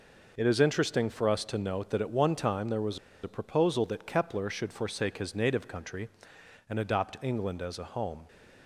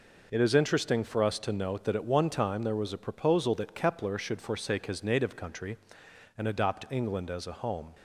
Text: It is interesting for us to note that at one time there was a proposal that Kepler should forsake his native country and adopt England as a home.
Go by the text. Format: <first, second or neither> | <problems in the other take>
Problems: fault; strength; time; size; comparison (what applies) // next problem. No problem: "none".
second | pauses between "was" and "a"; slight; at 2.9 s; 0.25 s long